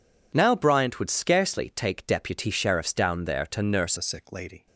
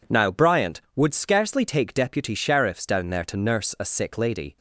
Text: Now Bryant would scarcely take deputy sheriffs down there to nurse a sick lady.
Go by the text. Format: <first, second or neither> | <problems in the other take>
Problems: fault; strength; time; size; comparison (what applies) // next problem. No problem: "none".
second | changes voice at "a"; from 3.9 s on; 0.7 s long